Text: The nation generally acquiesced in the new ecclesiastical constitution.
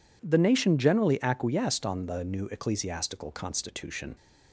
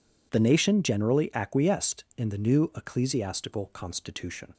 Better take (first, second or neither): second